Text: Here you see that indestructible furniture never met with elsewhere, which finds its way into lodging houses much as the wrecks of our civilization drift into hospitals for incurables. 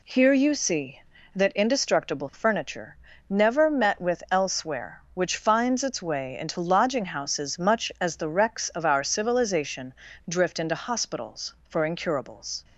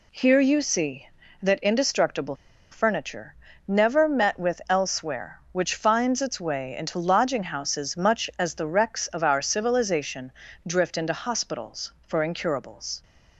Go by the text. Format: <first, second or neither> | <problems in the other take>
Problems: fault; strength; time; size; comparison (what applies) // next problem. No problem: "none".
first | pauses between "indestructible" and "furniture"; at 2.3 s; 0.36 s long // pauses between "furniture" and "never"; slight; at 3.3 s; 0.32 s long; slight in the first // pauses between "civilization" and "drift"; slight; at 10.3 s; 0.34 s long; slight in the first